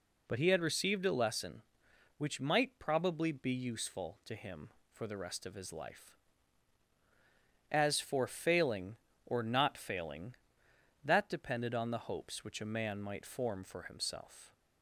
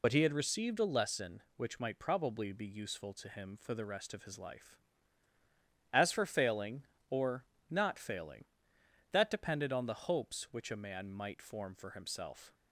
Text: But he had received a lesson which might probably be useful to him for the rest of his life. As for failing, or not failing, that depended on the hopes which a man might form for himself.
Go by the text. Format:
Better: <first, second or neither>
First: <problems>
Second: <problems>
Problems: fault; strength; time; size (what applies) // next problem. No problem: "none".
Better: first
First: none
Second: loses the start of "But"; at 0.0 s; 55 ms // pauses between "or" and "not"; slight; at 7.4 s; 0.26 s long